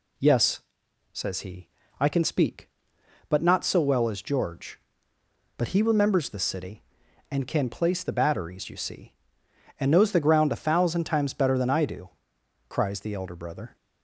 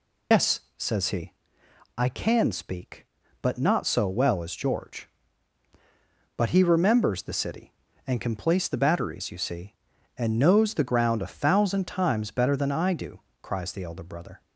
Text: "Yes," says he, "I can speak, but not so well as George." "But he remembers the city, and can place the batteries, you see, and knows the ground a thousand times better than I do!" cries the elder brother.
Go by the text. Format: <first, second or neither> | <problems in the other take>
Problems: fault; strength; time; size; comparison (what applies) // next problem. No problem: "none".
first | loses the start of "Yes"; at 0.3 s; 100 ms